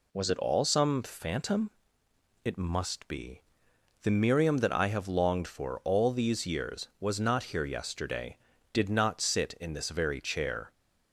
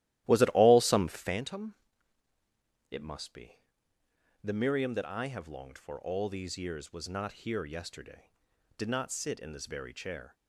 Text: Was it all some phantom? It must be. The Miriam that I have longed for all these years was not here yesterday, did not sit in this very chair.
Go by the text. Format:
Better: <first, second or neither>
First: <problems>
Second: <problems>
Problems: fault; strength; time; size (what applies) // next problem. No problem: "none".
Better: first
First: none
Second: starts louder than the rest; strong; until 1.4 s; 14.5 dB